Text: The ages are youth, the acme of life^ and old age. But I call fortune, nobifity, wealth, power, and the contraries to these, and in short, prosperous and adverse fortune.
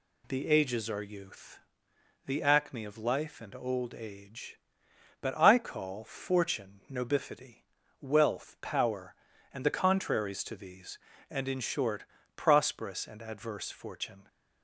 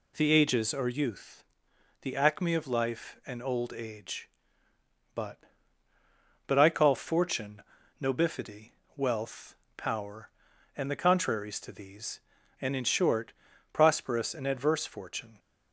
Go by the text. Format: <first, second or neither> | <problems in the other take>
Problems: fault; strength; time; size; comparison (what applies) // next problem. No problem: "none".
first | says "But" twice; at 6.4 s